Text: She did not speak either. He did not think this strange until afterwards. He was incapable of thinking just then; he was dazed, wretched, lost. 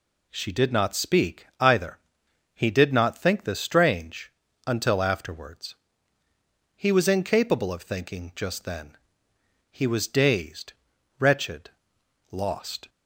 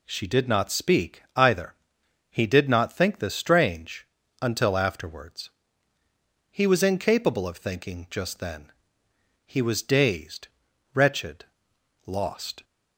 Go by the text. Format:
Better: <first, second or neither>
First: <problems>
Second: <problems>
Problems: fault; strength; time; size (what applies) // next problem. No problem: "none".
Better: neither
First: pauses between "strange" and "until"; slight; at 4.3 s; 0.36 s long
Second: pauses between "strange" and "until"; slight; at 4.0 s; 0.36 s long